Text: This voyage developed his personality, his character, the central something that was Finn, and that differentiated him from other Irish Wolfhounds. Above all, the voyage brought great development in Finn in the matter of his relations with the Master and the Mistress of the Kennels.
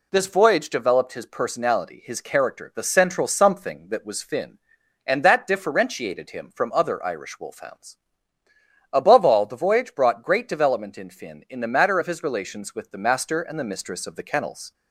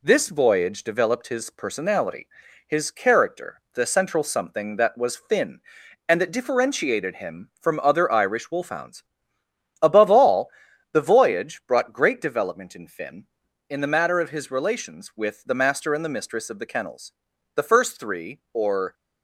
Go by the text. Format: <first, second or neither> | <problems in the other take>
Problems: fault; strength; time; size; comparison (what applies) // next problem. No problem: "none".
first | goes on to say "The first three or"; from 17.5 s on; 1.3 s long